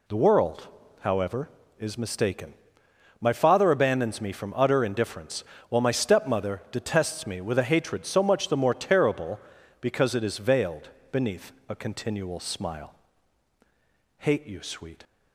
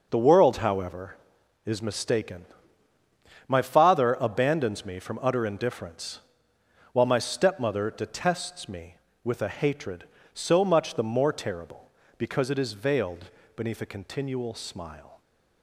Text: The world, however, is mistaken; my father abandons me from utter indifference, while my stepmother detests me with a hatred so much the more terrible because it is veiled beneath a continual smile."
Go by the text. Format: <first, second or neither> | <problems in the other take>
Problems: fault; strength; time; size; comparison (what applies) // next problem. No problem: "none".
second | pauses between "veiled" and "beneath"; slight; at 10.8 s; 0.22 s long; slight in the second // pauses between "beneath" and "a"; slight; at 11.5 s; 0.16 s long // goes on to say "Hate you sweet"; noticeable; from 14.1 s on; 0.84 s long